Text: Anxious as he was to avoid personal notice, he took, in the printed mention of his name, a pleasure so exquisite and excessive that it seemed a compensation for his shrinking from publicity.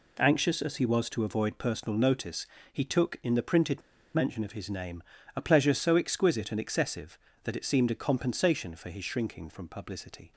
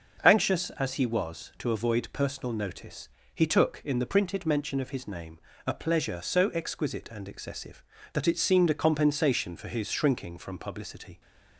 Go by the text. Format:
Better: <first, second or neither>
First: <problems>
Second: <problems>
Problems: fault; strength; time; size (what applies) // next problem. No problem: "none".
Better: second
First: pauses between "printed" and "mention"; slight; at 3.8 s; 0.32 s long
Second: none